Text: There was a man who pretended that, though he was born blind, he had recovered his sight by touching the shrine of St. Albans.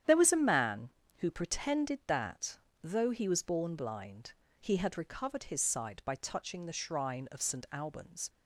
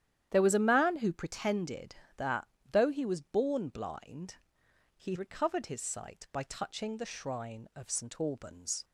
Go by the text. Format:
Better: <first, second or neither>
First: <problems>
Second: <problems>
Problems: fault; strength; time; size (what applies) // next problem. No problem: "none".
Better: first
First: starts louder than the rest; strong; until 1.3 s; 9.5 dB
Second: starts louder than the rest; strong; until 1.3 s; 10.5 dB // skips "had"; at 5.1 s